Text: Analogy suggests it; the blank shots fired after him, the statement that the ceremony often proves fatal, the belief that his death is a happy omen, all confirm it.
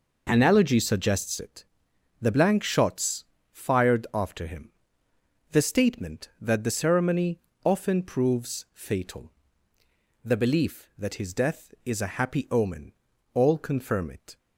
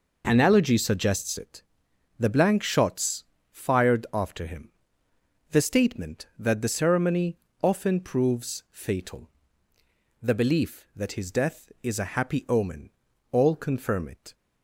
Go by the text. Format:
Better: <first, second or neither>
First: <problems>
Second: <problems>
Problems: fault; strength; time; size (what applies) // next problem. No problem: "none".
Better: neither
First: pauses between "shots" and "fired"; slight; at 3.2 s; 0.30 s long // pauses between "ceremony" and "often"; slight; at 7.3 s; 0.26 s long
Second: pauses between "shots" and "fired"; slight; at 3.2 s; 0.30 s long // pauses between "ceremony" and "often"; slight; at 7.3 s; 0.26 s long